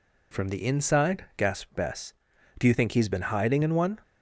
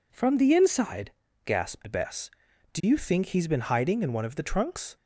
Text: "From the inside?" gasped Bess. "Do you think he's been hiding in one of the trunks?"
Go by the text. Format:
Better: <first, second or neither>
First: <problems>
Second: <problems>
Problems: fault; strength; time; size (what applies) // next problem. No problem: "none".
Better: second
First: stops before "of the trunks"; at 4.0 s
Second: none